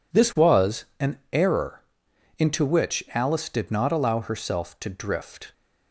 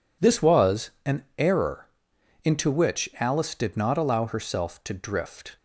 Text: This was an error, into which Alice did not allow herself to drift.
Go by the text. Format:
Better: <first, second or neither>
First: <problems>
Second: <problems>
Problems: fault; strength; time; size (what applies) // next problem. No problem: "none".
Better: neither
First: pauses between "was" and "an"; slight; at 0.8 s; 0.16 s long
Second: pauses between "was" and "an"; slight; at 0.9 s; 0.16 s long